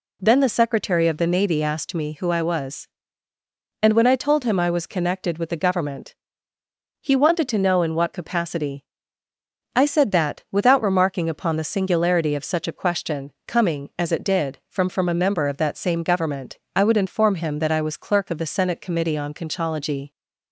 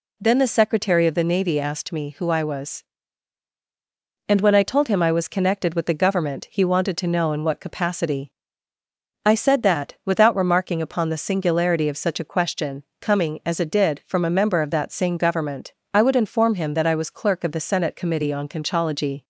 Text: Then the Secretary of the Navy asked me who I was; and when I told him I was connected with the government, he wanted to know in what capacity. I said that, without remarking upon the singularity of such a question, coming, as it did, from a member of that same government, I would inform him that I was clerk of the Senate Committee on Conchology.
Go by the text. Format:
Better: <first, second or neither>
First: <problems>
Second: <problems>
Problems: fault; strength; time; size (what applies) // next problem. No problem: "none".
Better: second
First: says "from" twice; at 14.9 s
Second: none